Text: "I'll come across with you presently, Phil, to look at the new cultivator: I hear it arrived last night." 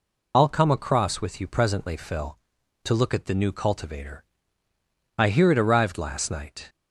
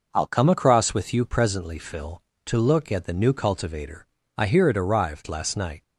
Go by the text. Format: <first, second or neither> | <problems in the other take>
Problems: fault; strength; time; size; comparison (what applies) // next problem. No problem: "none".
second | loses the start of "I'll"; at 0.3 s; 40 ms